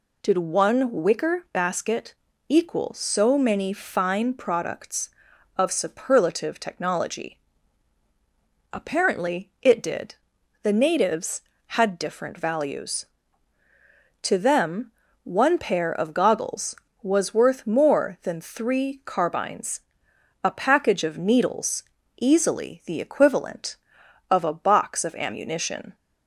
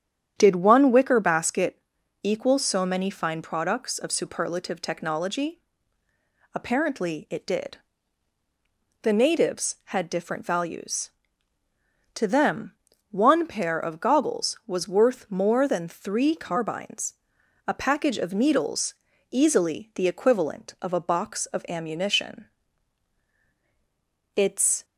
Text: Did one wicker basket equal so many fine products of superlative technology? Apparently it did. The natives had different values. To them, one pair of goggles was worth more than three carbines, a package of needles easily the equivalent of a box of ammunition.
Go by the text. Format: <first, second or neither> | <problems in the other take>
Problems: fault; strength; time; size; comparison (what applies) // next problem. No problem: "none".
first | starts louder than the rest; strong; until 1.3 s; 9 dB // pauses between "basket" and "equal"; at 1.8 s; 0.42 s long; slight in the first // pauses between "needles" and "easily"; at 18.9 s; 0.38 s long; also in the first // goes on to say "It's"; from 24.3 s on; 0.50 s long